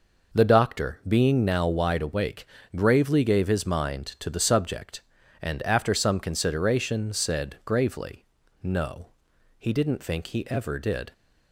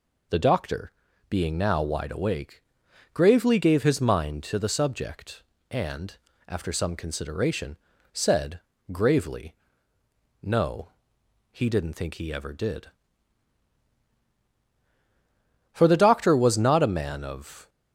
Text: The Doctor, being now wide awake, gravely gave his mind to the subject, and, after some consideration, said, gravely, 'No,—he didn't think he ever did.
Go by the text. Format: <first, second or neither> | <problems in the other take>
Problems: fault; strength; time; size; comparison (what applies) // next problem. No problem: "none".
first | goes on to say "For the Doctor was not a man of"; strong; from 15.7 s on; 1.9 s long